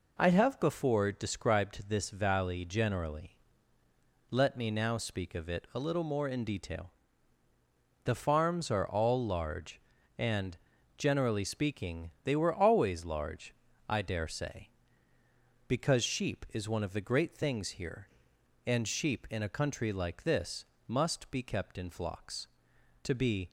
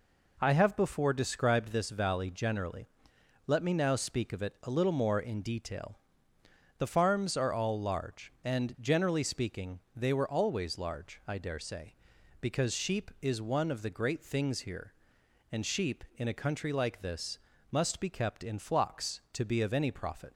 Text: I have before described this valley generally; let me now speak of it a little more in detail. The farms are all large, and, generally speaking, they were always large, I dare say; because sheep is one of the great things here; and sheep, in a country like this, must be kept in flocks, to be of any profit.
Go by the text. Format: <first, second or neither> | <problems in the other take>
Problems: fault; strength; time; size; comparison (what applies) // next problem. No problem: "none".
second | stops before "of any profit"; at 23.4 s